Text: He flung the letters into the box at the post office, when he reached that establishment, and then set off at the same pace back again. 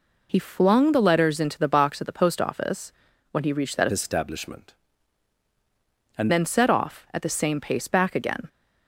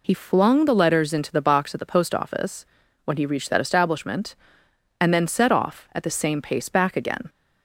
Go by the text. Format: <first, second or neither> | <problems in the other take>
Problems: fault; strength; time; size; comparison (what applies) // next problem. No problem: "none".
second | changes voice from "establishment" to "and"; from 3.9 to 6.3 s; 2.4 s long